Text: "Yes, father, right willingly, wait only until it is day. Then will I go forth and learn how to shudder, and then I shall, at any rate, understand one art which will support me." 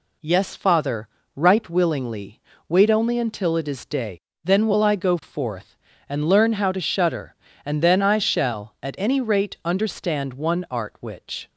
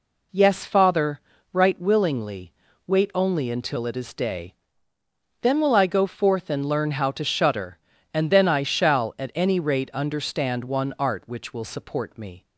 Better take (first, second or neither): second